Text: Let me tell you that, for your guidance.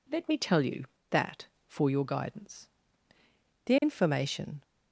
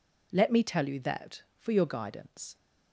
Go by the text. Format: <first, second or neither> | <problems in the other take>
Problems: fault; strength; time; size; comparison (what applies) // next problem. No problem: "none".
second | goes on to say "The information"; noticeable; from 3.6 s on; 0.95 s long